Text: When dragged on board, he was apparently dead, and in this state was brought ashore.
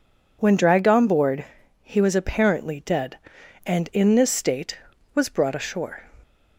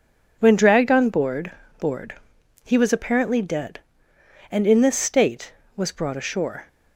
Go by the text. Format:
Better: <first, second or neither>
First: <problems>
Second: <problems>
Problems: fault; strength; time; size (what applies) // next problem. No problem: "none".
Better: first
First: none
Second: says "board" twice; at 1.7 s